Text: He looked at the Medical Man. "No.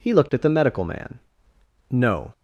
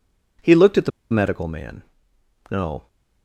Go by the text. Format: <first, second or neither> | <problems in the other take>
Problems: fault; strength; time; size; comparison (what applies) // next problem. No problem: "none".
first | pauses between "the" and "Medical"; slight; at 0.9 s; 0.22 s long